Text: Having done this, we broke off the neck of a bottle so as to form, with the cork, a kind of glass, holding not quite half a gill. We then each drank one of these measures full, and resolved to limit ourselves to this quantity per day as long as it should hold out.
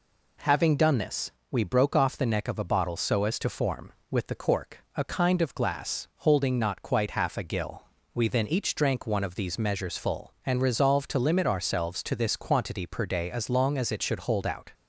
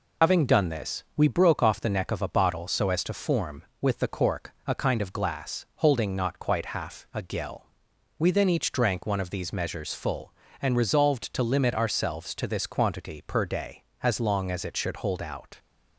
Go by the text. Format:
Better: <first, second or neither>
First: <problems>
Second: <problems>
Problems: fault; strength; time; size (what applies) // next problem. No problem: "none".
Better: first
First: none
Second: loses the start of "Having"; at 0.2 s; 80 ms